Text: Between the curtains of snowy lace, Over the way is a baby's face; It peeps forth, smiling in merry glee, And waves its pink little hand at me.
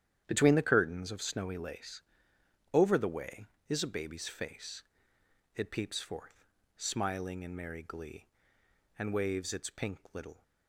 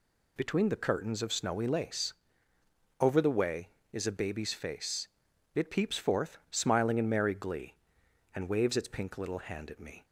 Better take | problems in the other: second | starts louder than the rest; strong; until 1.2 s; 10 dB // pauses between "pink" and "little"; slight; at 9.9 s; 0.16 s long // stops before "hand at me"; at 10.4 s

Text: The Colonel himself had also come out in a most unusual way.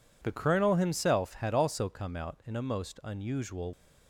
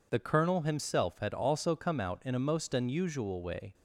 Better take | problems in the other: second | stops before "way"; at 3.7 s

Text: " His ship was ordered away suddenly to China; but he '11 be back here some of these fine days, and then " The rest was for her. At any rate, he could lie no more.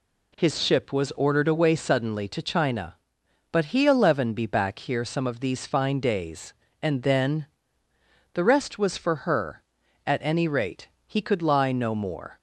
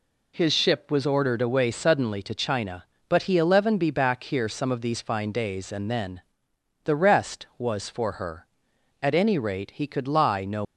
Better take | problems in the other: first | stops before "more"; at 10.6 s

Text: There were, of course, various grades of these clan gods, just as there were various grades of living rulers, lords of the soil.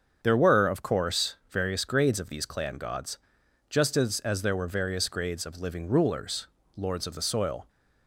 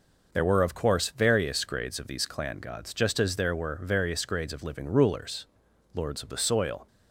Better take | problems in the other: second | starts louder than the rest; strong; until 1.2 s; 7.5 dB // says "as" twice; at 4.1 s

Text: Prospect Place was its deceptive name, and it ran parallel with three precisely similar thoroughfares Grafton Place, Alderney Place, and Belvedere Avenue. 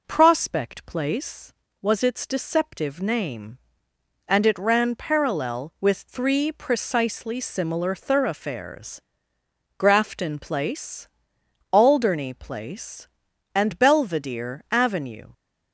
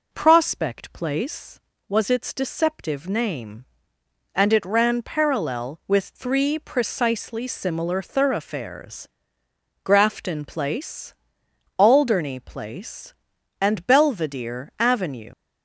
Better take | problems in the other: first | pauses between "thoroughfares" and "Grafton"; noticeable; at 9.0 s; 0.75 s long; noticeable in the first // leaves "Avenue" unfinished; at 15.3 s; 75 ms

